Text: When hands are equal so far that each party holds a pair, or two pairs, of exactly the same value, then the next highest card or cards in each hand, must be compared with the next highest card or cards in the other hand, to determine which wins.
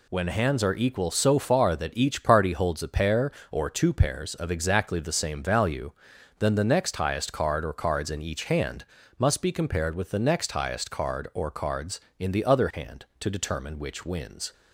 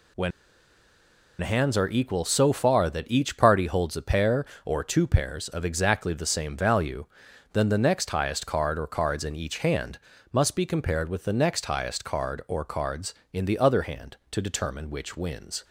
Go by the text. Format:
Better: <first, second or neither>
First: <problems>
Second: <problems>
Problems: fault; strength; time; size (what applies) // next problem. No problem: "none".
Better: first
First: none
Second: pauses between "When" and "hands"; at 0.3 s; 1.1 s long